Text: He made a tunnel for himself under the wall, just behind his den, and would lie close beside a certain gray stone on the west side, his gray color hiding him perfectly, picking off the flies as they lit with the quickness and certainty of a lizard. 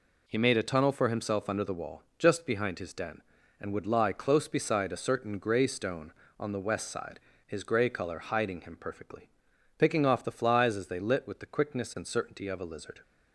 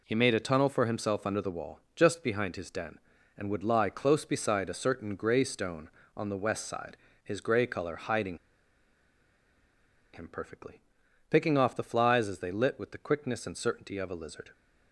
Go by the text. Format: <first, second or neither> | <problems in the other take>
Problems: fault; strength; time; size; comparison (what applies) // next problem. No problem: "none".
first | pauses between "hiding" and "him"; strong; at 8.3 s; 1.7 s long